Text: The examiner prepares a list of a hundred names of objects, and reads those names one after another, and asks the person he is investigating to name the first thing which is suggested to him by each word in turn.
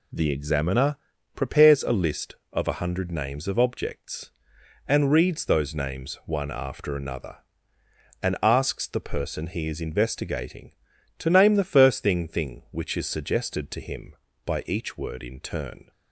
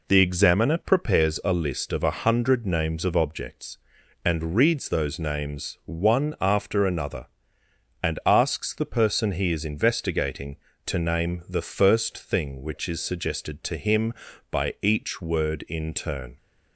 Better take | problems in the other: second | pauses between "examiner" and "prepares"; at 0.9 s; 0.38 s long // says "thing" twice; at 12.2 s

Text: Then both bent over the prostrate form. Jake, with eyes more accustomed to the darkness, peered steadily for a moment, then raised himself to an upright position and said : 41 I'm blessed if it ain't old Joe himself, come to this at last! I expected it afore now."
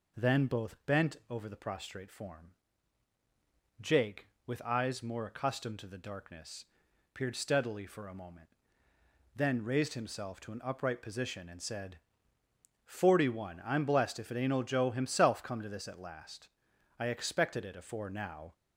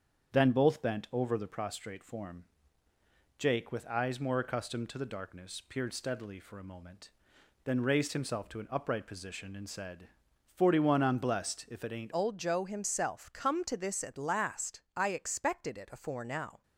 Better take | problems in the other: first | starts louder than the rest; strong; until 1.3 s; 7.5 dB // changes voice at "old"; from 12.1 s on; 4.5 s long

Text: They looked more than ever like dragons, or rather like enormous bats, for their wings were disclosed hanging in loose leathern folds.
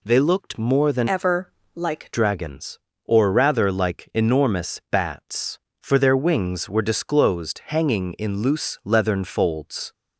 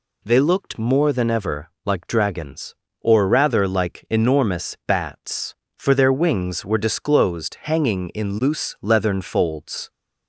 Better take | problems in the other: second | changes voice from "ever" to "like"; from 1.0 to 2.1 s; 1.1 s long // pauses between "ever" and "like"; slight; at 1.4 s; 0.26 s long; slight in the second

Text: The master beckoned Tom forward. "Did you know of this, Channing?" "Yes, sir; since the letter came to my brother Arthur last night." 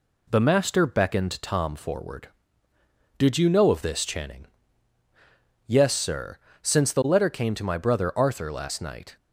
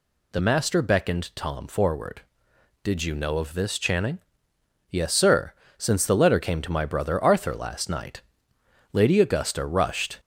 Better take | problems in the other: first | goes on to say "Lady Augusta rushed"; noticeable; from 8.9 s on; 1.2 s long

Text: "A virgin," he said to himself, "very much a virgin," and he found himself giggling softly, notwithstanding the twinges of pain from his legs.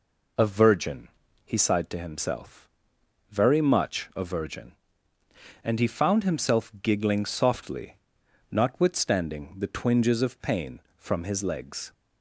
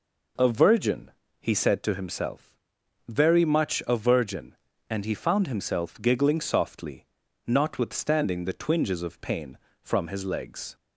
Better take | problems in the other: second | says "sighed" for "said"; at 1.5 s

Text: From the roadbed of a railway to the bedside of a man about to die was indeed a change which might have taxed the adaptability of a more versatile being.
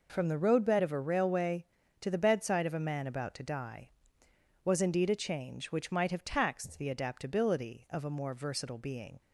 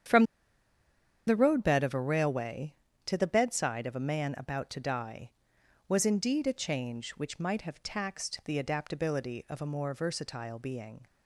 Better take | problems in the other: first | starts louder than the rest; strong; until 2.1 s; 8.5 dB // pauses between "From" and "the"; at 0.2 s; 1.0 s long

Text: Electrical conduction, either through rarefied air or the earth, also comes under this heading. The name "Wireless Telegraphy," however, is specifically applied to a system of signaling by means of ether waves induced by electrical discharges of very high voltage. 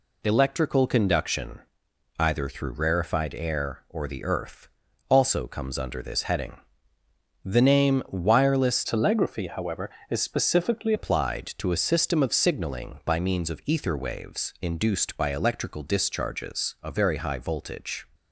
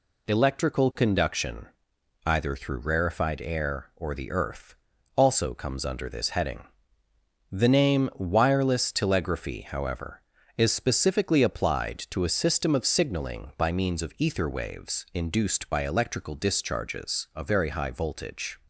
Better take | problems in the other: second | changes voice from "Telegraphy" to "specifically"; from 8.8 to 10.9 s; 2.1 s long

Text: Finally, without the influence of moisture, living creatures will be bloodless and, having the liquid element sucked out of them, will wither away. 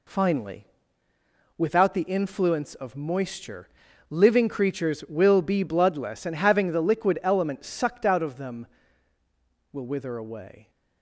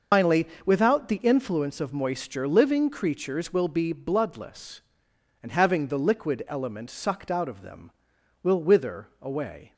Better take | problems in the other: first | loses the start of "Finally"; at 0.1 s; 115 ms

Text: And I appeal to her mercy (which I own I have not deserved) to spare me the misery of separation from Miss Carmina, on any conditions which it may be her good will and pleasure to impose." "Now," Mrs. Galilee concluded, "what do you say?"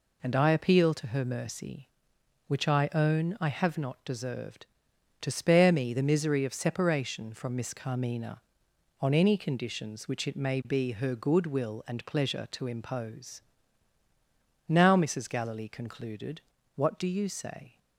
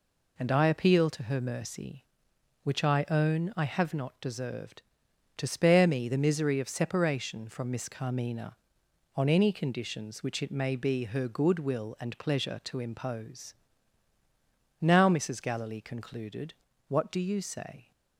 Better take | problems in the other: neither | none

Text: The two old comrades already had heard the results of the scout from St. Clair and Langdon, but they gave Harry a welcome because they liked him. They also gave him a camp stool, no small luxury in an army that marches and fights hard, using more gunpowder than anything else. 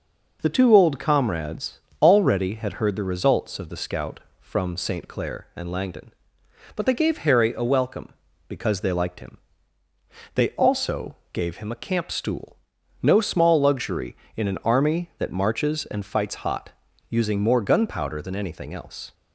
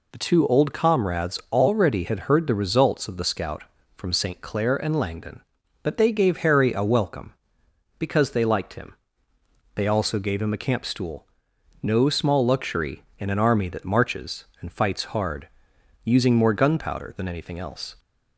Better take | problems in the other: second | pauses between "comrades" and "already"; slight; at 1.7 s; 0.20 s long // pauses between "also" and "gave"; slight; at 11.1 s; 0.16 s long // says "hot" for "hard"; at 16.3 s

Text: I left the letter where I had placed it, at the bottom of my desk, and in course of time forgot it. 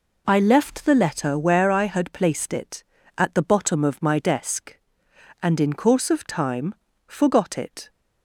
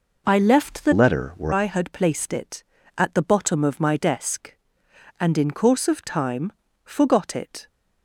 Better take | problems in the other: first | changes voice from "letter" to "where"; from 0.9 to 1.5 s; 0.6 s long // pauses between "time" and "forgot"; slight; at 6.5 s; 0.32 s long; slight in the first

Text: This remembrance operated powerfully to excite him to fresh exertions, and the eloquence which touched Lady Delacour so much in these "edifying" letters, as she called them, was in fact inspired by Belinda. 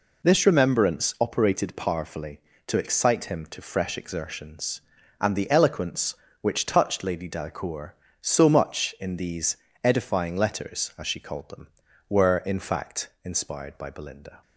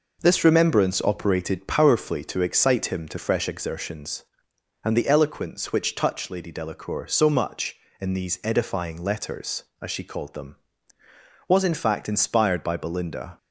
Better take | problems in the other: second | pauses between "these" and "edifying"; slight; at 9.5 s; 0.28 s long // says "were" for "was"; at 12.0 s

